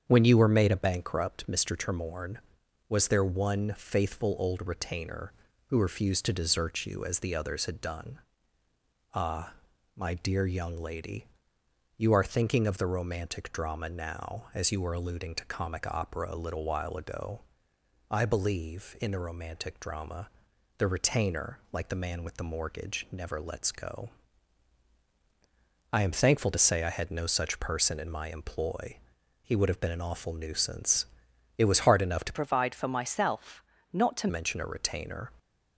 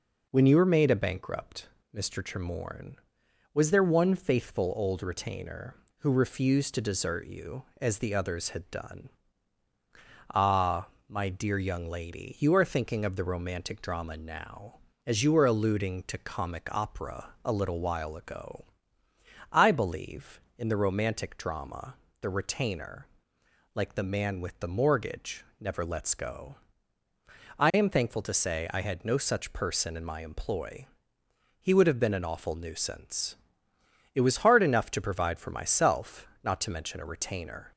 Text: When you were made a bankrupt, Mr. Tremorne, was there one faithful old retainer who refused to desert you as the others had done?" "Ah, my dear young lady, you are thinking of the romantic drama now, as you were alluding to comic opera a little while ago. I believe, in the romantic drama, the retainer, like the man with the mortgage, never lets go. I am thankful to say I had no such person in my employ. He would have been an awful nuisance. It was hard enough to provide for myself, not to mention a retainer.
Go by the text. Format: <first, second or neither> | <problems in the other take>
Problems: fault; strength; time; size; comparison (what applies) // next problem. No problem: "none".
second | starts louder than the rest; strong; until 1.1 s; 7.5 dB // changes voice from "provide" to "to"; from 32.3 to 34.2 s; 1.9 s long